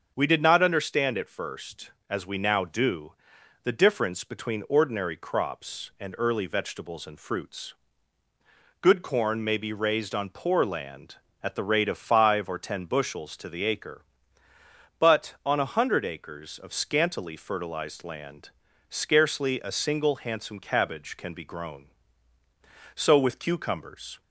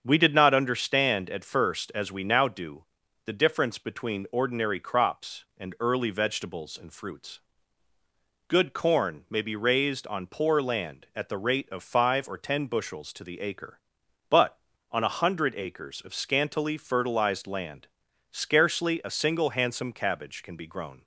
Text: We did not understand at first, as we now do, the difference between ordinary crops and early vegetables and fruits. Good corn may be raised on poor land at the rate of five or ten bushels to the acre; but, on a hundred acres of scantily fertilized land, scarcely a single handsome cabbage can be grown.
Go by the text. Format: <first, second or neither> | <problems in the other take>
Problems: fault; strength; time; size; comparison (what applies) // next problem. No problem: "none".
second | starts louder than the rest; until 1.1 s; 6.5 dB; also in the second // goes on to say "So with cucumbers"; noticeable; from 22.9 s on; 1.2 s long